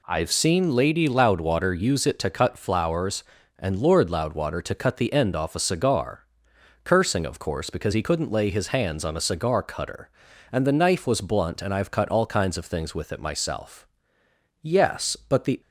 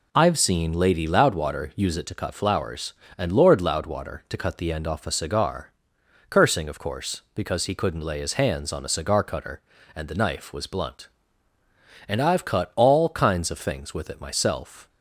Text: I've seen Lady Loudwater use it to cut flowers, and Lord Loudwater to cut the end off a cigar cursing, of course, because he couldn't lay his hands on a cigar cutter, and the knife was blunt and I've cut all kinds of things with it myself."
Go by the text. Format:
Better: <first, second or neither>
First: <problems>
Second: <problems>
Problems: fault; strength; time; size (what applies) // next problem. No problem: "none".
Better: second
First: pauses between "cigar" and "cursing"; noticeable; at 6.2 s; 0.58 s long // goes on to say "Yes but the"; noticeable; from 14.6 s on; 0.98 s long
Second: pauses between "cigar" and "cursing"; noticeable; at 5.7 s; 0.60 s long